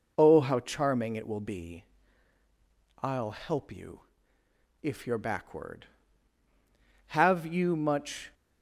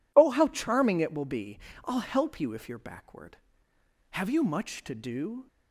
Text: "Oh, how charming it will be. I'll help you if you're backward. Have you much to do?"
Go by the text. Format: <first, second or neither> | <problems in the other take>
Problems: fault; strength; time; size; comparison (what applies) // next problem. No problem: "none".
second | pauses between "you" and "if"; noticeable; at 4.0 s; 0.82 s long // stops before "to do"; at 8.3 s